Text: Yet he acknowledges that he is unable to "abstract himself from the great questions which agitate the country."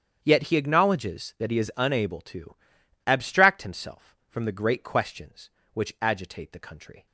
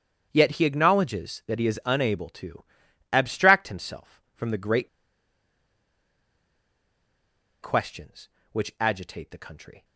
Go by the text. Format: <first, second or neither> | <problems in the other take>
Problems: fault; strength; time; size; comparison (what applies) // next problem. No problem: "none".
first | starts louder than the rest; strong; until 1.3 s; 8 dB; strong in the first // pauses between "to" and "abstract"; noticeable; at 2.6 s; 0.50 s long; noticeable in the first // pauses between "great" and "questions"; strong; at 4.8 s; 2.7 s long